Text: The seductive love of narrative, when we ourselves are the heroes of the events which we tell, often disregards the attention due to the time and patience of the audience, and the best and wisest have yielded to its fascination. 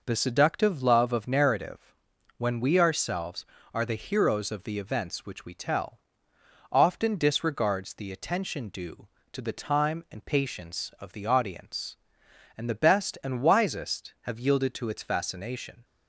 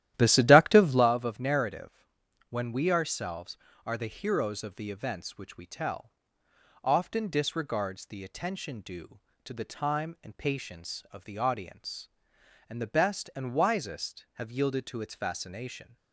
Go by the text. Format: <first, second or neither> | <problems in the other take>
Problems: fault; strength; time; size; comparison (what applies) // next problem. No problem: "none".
first | starts louder than the rest; strong; until 1.1 s; 13 dB